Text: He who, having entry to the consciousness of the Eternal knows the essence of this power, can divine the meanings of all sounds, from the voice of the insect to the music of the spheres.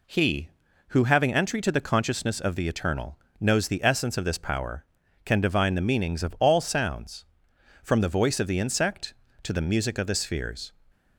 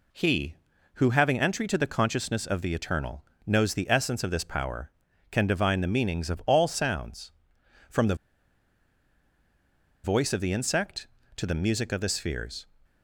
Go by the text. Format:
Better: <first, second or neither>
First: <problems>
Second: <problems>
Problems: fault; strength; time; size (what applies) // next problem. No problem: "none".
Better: first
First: pauses between "Eternal" and "knows"; slight; at 3.1 s; 0.22 s long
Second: pauses between "Eternal" and "knows"; slight; at 3.2 s; 0.22 s long // pauses between "the" and "voice"; strong; at 8.1 s; 1.8 s long